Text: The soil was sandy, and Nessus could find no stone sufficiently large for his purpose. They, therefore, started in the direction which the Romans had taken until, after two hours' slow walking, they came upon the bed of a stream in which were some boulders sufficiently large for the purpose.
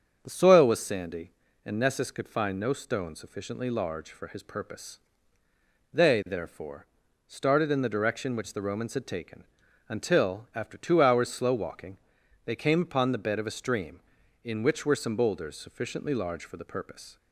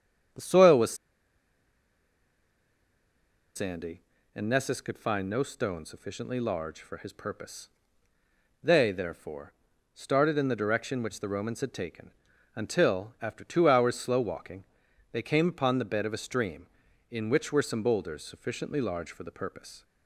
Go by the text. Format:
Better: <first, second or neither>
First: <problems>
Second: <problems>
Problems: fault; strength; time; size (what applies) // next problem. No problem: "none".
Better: first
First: starts louder than the rest; until 1.2 s; 7 dB // pauses between "taken" and "until"; noticeable; at 9.4 s; 0.46 s long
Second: starts louder than the rest; until 3.9 s; 7 dB // pauses between "was" and "sandy"; strong; at 0.9 s; 2.6 s long // pauses between "taken" and "until"; noticeable; at 12.0 s; 0.46 s long